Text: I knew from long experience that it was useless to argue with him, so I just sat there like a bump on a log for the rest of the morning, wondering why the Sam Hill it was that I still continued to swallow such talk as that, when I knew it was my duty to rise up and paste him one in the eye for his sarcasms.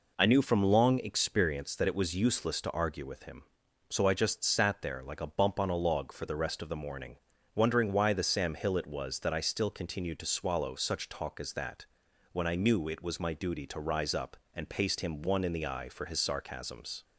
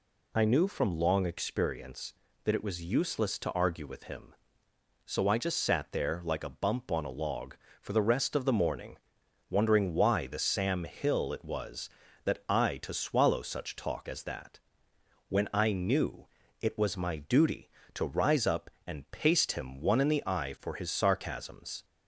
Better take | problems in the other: first | skips "still continued"; at 12.7 s // pauses between "knew" and "it"; at 16.2 s; 0.38 s long

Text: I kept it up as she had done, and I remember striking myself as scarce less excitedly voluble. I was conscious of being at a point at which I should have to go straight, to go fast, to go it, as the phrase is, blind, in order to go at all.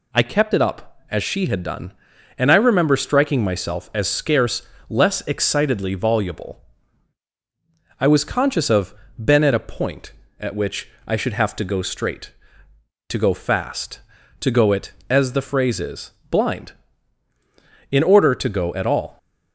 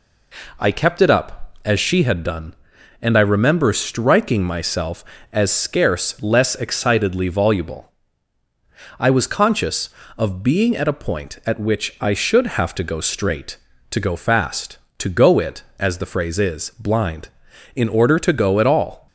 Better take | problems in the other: second | pauses between "scarce" and "less"; slight; at 4.6 s; 0.30 s long // says "been" for "being"; at 9.2 s // pauses between "which" and "I"; slight; at 10.8 s; 0.18 s long

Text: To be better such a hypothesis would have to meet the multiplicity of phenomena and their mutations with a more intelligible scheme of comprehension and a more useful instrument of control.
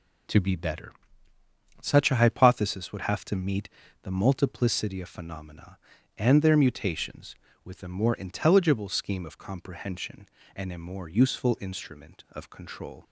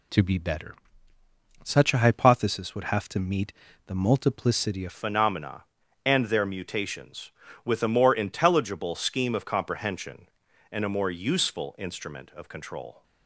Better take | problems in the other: first | pauses between "better" and "such"; noticeable; at 0.7 s; 0.88 s long; noticeable in the first // pauses between "meet" and "the"; slight; at 3.5 s; 0.36 s long; slight in the first // changes voice at "phenomena"; from 4.9 s on; 8.1 s long

